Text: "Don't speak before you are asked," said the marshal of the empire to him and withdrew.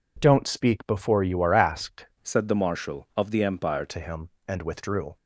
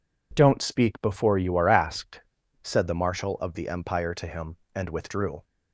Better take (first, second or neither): second